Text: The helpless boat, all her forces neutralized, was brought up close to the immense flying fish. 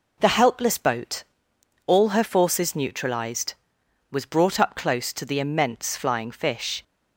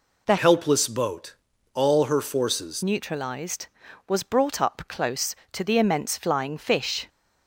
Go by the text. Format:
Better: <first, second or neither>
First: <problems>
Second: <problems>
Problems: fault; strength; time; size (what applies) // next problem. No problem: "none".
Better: first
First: none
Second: changes voice from "helpless" to "forces"; from 0.3 to 2.8 s; 2.5 s long